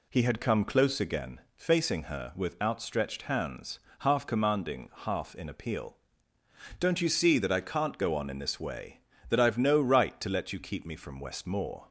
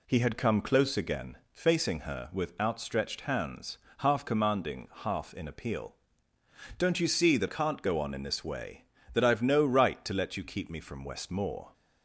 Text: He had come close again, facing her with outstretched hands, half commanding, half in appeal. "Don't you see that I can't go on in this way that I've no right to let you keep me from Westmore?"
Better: first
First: none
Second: skips "I"; at 7.4 s

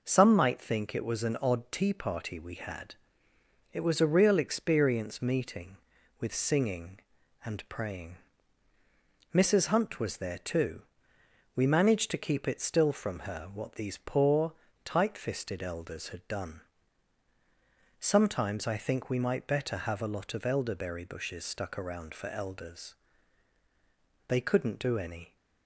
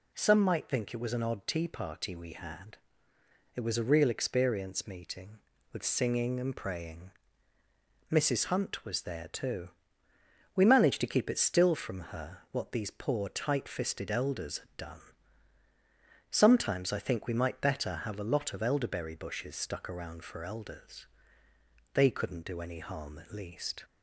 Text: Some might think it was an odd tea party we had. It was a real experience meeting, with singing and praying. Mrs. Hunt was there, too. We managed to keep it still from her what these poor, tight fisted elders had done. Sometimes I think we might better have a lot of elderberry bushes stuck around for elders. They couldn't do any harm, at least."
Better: second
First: stops before "harm at least"; at 25.3 s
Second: none

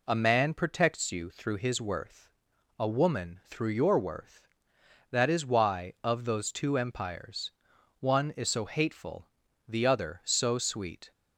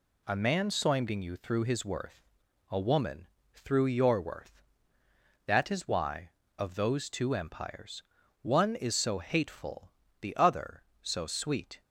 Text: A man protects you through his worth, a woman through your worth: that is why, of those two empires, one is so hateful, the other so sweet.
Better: first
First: none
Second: says "soimding" for "protects"; at 0.6 s // pauses between "woman" and "through"; slight; at 3.2 s; 0.28 s long

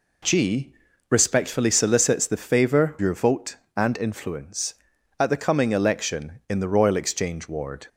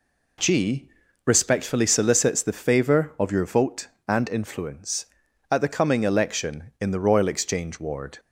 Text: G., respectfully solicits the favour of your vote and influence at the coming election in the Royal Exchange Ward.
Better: second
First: skips "of"; at 2.9 s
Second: none

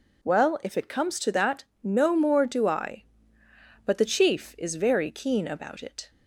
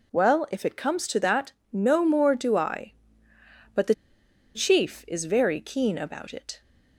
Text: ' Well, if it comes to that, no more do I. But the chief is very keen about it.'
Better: first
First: none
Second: pauses between "the" and "chief"; noticeable; at 3.9 s; 0.60 s long

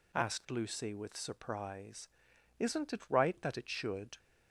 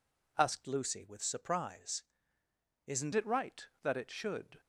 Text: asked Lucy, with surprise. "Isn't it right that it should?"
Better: first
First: none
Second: changes voice from "Lucy" to "Isn't"; from 0.6 to 3.1 s; 2.5 s long

